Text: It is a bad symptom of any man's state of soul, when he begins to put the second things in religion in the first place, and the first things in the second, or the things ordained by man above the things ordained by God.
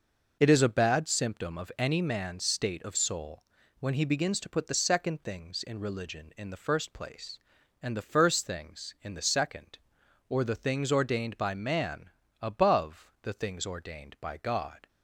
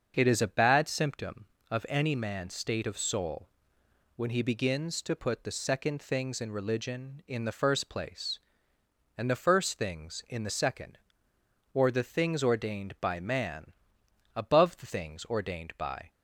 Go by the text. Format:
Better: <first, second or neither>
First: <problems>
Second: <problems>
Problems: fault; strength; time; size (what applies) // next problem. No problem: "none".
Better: first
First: pauses between "man" and "above"; slight; at 12.1 s; 0.30 s long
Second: starts louder than the rest; until 1.1 s; 6.5 dB // pauses between "man" and "above"; noticeable; at 13.7 s; 0.64 s long // stops before "God"; at 16.0 s